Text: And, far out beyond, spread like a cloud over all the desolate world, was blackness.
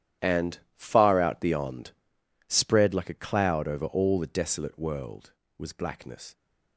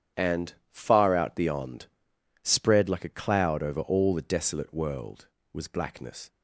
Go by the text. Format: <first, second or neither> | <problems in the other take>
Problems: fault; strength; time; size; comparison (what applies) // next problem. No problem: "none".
second | gets quieter; strong; throughout; 14.5 dB // starts louder than the rest; strong; until 1.3 s; 10.5 dB; strong in the second